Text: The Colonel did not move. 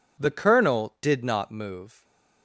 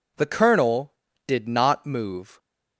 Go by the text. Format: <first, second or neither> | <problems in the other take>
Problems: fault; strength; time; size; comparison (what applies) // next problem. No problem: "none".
neither | none